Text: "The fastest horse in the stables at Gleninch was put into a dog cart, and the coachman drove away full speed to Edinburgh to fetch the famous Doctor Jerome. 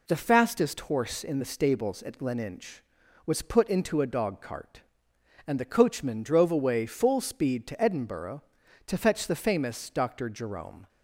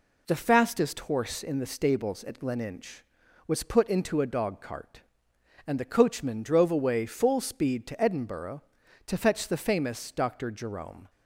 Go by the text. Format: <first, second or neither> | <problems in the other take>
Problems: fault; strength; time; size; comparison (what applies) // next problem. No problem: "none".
neither | none